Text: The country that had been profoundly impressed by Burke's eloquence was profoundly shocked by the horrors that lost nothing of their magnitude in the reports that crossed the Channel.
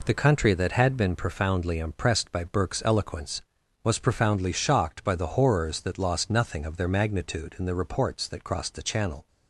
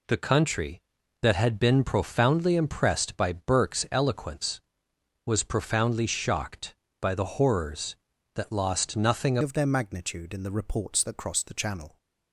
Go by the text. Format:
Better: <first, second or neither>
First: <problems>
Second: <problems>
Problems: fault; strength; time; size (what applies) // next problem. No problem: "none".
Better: first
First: none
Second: changes voice at "of"; from 9.4 s on; 2.5 s long